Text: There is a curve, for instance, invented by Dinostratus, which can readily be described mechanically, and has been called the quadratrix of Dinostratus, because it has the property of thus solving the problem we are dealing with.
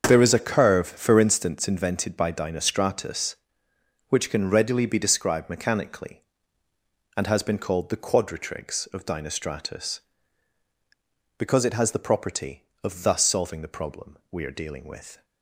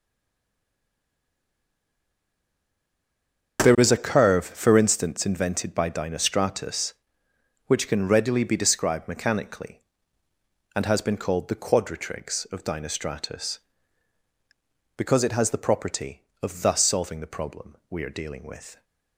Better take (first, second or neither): first